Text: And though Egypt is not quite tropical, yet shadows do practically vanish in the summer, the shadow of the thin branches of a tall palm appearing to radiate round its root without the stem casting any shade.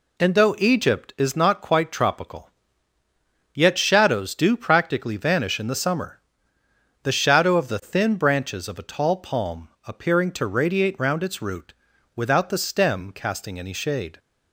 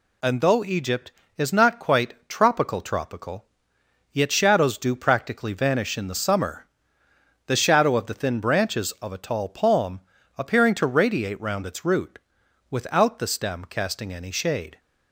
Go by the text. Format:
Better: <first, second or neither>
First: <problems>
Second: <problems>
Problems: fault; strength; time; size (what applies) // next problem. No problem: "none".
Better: first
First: pauses between "palm" and "appearing"; slight; at 9.6 s; 0.18 s long // pauses between "root" and "without"; at 11.7 s; 0.42 s long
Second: says "tropical" twice; at 2.8 s // pauses between "palm" and "appearing"; slight; at 10.0 s; 0.36 s long // pauses between "root" and "without"; noticeable; at 12.1 s; 0.52 s long